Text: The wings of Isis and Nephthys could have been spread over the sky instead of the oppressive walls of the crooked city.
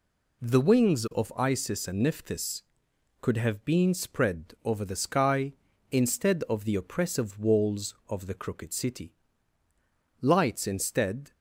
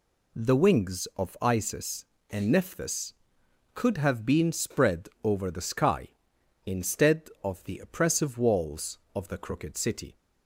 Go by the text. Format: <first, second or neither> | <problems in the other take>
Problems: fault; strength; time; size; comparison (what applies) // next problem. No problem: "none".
second | goes on to say "Lights instead"; noticeable; from 10.2 s on; 1.1 s long